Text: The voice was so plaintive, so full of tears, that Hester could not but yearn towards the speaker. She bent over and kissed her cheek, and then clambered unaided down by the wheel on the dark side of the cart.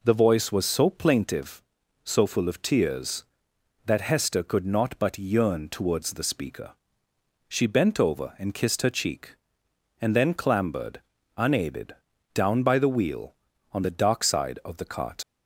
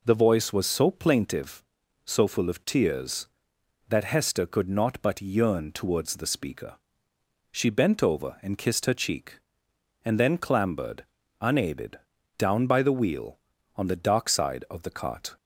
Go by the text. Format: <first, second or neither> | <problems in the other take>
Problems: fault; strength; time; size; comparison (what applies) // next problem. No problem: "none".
second | pauses between "clambered" and "unaided"; slight; at 11.0 s; 0.36 s long; slight in the second // pauses between "unaided" and "down"; at 11.9 s; 0.42 s long; also in the second // leaves "cart" unfinished; at 15.2 s; 80 ms